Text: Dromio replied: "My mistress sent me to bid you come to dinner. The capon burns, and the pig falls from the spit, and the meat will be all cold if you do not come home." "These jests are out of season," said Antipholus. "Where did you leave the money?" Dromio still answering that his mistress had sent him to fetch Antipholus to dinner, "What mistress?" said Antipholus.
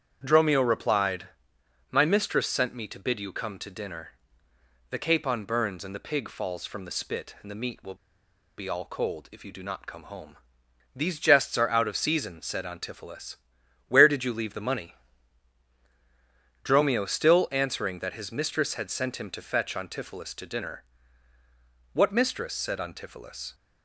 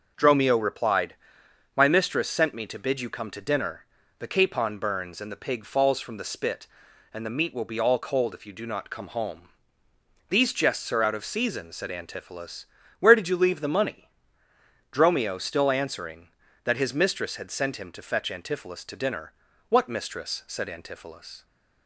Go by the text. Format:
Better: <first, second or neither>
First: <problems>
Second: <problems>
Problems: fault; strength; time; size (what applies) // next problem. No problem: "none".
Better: second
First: starts louder than the rest; strong; until 1.2 s; 8.5 dB // pauses between "will" and "be"; noticeable; at 7.9 s; 0.61 s long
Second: none